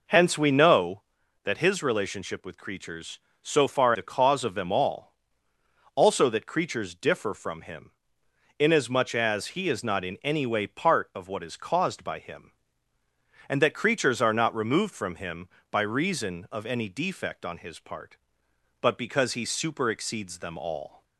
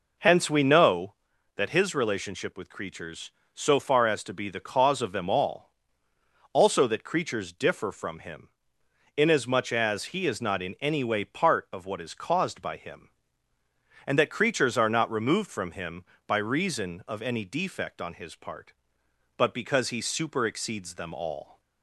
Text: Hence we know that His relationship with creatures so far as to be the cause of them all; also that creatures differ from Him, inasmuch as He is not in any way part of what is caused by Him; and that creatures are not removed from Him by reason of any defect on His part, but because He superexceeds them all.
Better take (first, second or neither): second